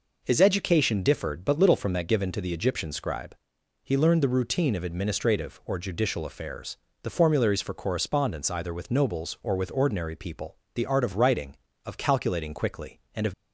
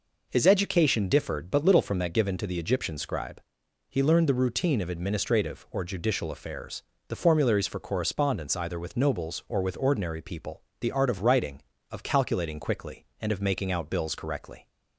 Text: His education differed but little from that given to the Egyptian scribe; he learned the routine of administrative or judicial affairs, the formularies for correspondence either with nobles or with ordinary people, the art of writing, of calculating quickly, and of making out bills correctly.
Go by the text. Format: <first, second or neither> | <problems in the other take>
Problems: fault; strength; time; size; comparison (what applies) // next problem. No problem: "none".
second | stops before "making out bills correctly"; at 13.3 s